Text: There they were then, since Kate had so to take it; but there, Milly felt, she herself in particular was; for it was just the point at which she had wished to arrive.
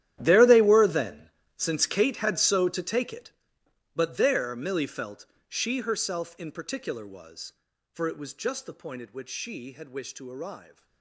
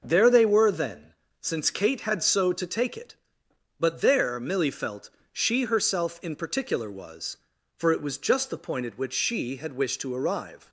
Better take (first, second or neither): second